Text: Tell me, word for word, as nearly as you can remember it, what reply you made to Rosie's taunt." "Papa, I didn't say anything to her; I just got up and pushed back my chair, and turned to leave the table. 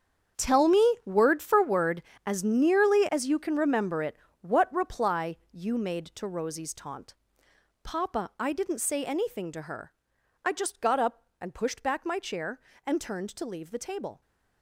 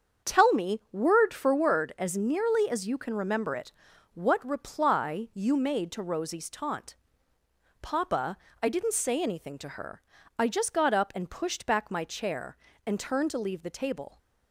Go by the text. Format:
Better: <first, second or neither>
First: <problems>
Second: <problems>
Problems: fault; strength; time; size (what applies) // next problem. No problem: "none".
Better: second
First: gets quieter; strong; throughout; 14 dB // starts louder than the rest; strong; until 1.5 s; 8 dB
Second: starts louder than the rest; strong; until 1.3 s; 7.5 dB